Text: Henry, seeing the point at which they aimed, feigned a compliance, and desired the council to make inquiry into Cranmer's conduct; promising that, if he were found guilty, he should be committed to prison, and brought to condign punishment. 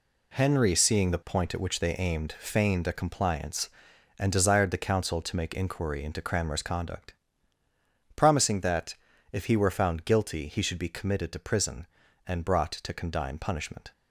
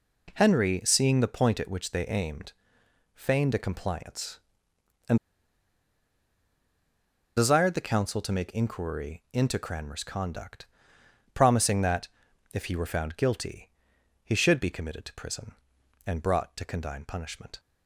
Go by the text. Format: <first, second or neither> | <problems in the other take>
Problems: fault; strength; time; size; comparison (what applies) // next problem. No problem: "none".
first | pauses between "and" and "desired"; strong; at 5.1 s; 2.1 s long